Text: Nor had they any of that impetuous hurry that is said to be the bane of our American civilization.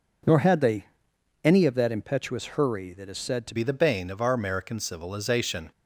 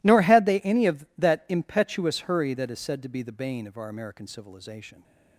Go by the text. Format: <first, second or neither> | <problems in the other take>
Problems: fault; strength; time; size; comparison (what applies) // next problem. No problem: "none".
second | pauses between "they" and "any"; noticeable; at 0.8 s; 0.56 s long // changes voice at "be"; from 3.5 s on; 2.2 s long